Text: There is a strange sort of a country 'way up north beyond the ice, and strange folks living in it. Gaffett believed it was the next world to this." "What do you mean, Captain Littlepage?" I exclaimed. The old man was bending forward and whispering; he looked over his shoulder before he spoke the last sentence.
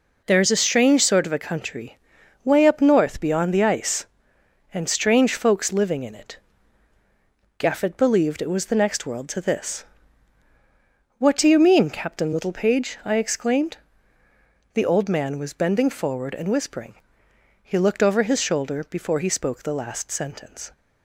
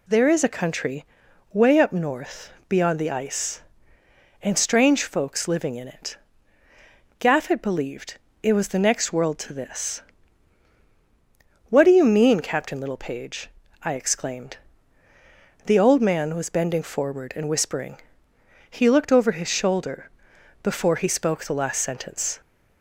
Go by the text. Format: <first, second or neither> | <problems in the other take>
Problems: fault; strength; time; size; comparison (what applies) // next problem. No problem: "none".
first | skips "a strange sort of"; at 0.4 s // pauses between "country" and "way"; noticeable; at 1.0 s; 0.48 s long; noticeable in the first // pauses between "north" and "beyond"; slight; at 2.5 s; 0.18 s long // pauses between "believed" and "it"; slight; at 8.1 s; 0.24 s long // pauses between "shoulder" and "before"; noticeable; at 20.1 s; 0.50 s long